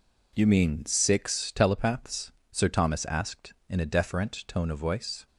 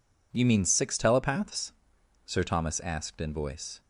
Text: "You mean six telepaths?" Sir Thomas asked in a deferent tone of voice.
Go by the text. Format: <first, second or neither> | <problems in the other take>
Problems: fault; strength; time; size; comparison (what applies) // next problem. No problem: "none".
first | skips "a deferent tone of"; at 3.3 s